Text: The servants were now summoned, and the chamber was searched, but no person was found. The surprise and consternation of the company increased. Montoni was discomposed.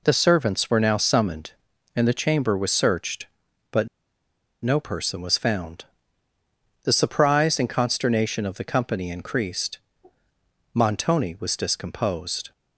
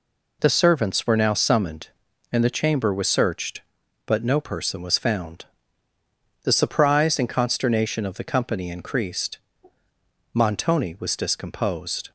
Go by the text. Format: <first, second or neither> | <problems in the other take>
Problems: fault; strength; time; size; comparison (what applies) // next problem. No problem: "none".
second | pauses between "but" and "no"; noticeable; at 3.8 s; 0.75 s long